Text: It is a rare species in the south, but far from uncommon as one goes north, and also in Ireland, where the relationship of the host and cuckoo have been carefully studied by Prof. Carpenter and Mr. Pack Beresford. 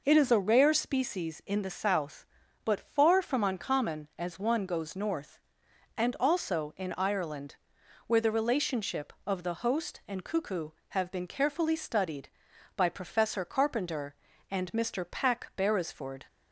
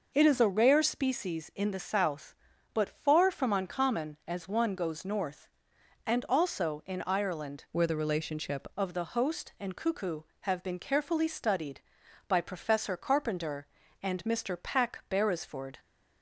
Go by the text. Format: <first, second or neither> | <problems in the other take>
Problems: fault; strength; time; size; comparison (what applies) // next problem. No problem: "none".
first | changes voice from "where" to "relationship"; from 7.7 to 8.6 s; 0.9 s long